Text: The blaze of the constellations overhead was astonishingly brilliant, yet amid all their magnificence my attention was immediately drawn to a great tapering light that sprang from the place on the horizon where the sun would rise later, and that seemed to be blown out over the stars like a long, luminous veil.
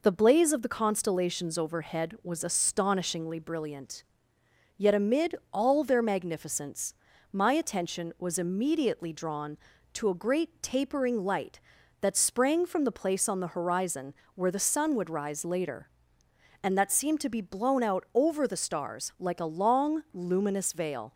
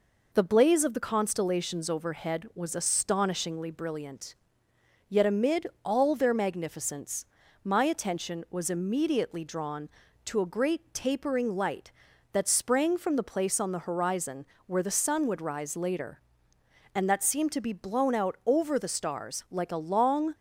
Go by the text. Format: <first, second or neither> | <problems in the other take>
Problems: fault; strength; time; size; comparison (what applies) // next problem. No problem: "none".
first | pauses between "amid" and "all"; slight; at 5.6 s; 0.18 s long; slight in the first // pauses between "magnificence" and "my"; at 7.2 s; 0.38 s long; also in the first // pauses between "horizon" and "where"; slight; at 14.4 s; 0.20 s long; slight in the first // stops before "luminous veil"; at 20.3 s